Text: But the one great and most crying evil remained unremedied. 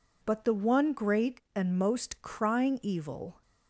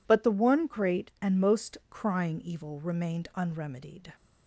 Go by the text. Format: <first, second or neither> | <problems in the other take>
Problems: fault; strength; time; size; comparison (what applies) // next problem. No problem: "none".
second | stops before "remained unremedied"; at 3.4 s